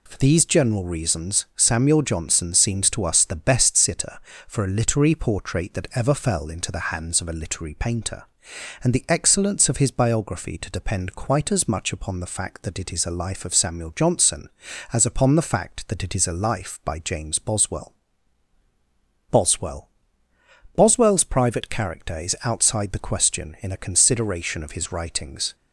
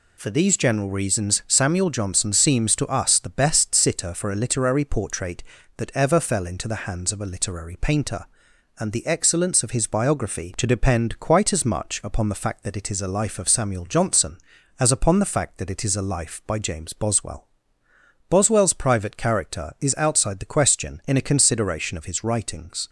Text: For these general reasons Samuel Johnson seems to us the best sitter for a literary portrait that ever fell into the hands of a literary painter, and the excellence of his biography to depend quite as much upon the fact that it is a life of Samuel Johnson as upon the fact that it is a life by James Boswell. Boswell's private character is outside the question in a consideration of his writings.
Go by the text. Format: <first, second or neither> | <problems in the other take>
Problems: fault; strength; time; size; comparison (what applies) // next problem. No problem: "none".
second | says "Boswell" twice; at 19.3 s